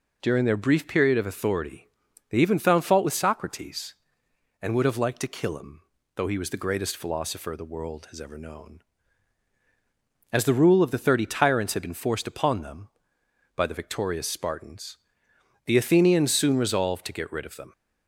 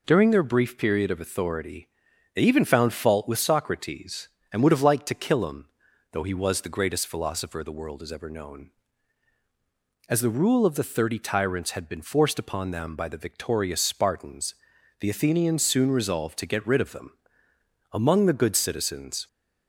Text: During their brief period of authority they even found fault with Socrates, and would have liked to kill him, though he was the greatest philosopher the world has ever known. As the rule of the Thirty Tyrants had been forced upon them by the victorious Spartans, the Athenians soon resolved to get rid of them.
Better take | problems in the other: first | pauses between "authority" and "they"; noticeable; at 1.8 s; 0.46 s long; also in the first // goes on to say "Among the good citizens"; from 17.9 s on; 1.3 s long

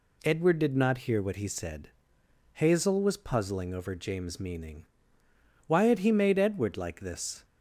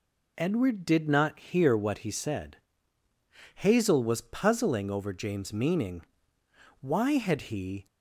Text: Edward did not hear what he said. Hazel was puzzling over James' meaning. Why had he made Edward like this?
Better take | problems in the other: first | stops before "made Edward like this"; at 7.8 s

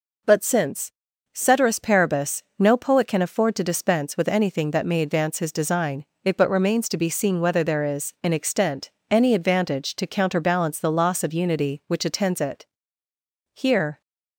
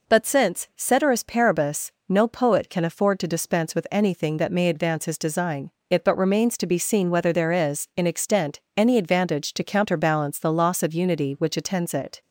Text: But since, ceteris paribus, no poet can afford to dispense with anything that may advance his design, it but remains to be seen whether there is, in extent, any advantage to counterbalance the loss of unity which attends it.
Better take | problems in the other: second | goes on to say "Here"; slight; from 13.5 s on; 0.48 s long

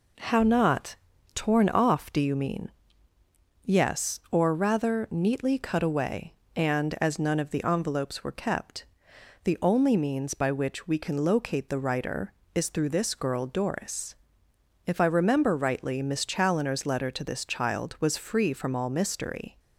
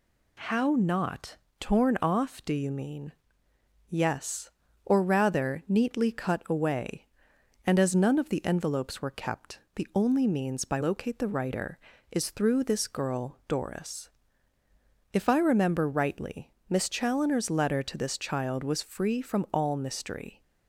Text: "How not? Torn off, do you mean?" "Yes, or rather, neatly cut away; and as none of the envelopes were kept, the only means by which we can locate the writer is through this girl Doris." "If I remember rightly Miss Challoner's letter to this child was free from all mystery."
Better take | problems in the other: first | skips "which we can"; at 10.8 s // pauses between "rightly" and "Miss"; slight; at 16.5 s; 0.16 s long

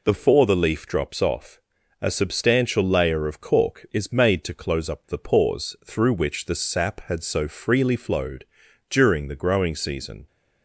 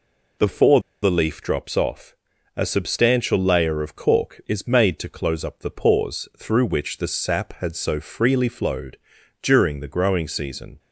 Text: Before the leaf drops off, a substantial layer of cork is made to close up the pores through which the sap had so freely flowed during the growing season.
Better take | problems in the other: first | pauses between "Before" and "the"; slight; at 0.7 s; 0.22 s long // pauses between "flowed" and "during"; at 8.9 s; 0.44 s long; also in the first

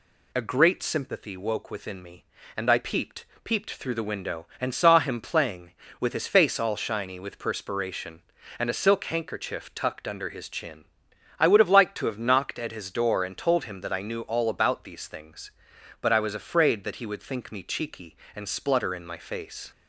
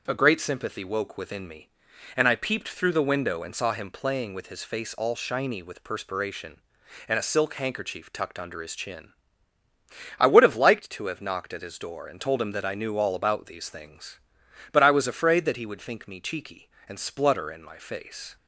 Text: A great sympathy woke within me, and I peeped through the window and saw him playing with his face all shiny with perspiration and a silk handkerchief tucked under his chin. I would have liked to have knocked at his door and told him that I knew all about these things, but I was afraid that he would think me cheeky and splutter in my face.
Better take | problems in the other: second | says "peeped" twice; at 3.4 s

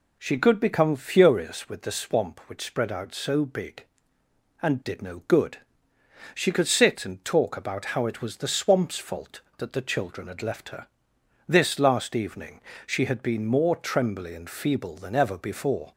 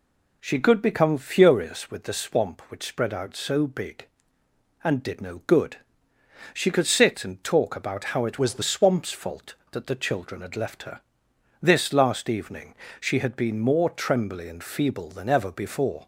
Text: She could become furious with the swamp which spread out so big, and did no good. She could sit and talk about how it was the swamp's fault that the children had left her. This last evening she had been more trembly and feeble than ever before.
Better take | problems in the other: first | changes voice from "was" to "the"; from 8.3 to 8.6 s; 0.3 s long // pauses between "evening" and "she"; slight; at 12.7 s; 0.26 s long; slight in the first

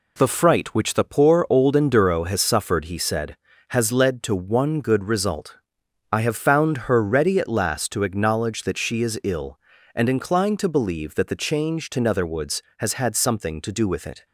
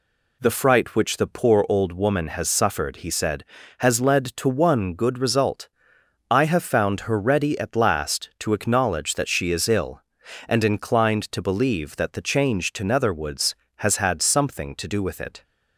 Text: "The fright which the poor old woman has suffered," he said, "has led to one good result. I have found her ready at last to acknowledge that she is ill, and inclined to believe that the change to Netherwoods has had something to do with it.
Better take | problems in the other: second | says "enduro" for "woman"; at 1.7 s

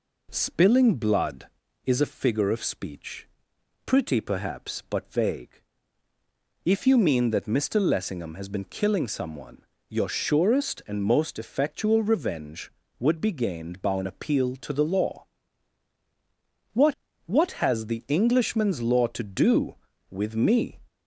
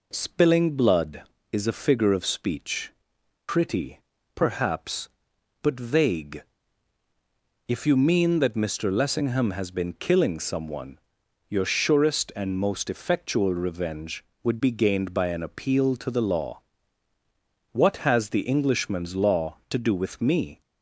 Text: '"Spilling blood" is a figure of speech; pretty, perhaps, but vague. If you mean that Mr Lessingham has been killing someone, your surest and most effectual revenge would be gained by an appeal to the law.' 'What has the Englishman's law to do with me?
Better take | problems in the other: second | says "What" twice; at 17.2 s

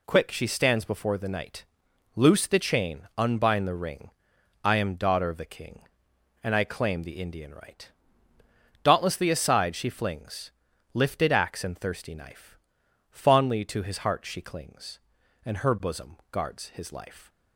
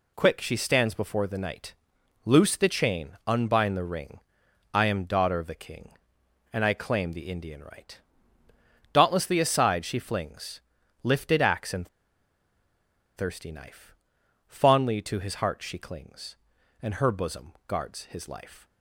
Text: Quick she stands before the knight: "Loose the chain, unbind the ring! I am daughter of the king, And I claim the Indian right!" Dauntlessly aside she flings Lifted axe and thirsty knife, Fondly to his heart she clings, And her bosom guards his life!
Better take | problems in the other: first | pauses between "flings" and "Lifted"; at 10.5 s; 0.42 s long; also in the first // pauses between "and" and "thirsty"; strong; at 11.8 s; 1.2 s long // pauses between "bosom" and "guards"; slight; at 17.5 s; 0.16 s long; slight in the first

